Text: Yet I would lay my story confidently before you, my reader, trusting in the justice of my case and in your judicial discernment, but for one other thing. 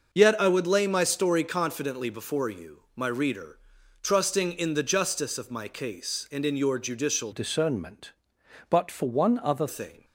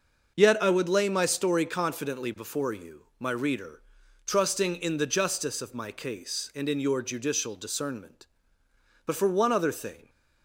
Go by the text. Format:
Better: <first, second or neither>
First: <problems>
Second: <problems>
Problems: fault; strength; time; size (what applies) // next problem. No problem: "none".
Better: second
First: starts louder than the rest; noticeable; until 1.1 s; 6 dB // changes voice from "discernment" to "other"; from 7.3 to 9.6 s; 2.3 s long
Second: starts louder than the rest; noticeable; until 1.3 s; 6 dB